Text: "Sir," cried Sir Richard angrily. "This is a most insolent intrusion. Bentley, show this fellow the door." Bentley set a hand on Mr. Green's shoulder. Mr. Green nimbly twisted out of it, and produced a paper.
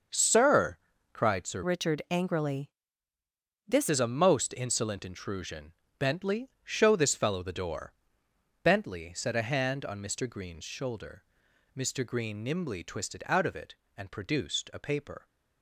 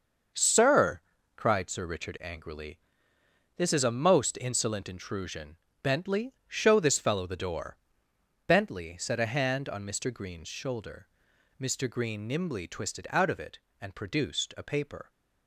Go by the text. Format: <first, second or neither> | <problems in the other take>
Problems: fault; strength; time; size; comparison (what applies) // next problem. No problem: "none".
second | starts louder than the rest; until 1.4 s; 6.5 dB; also in the second // changes voice from "Richard" to "This"; from 1.6 to 3.8 s; 2.2 s long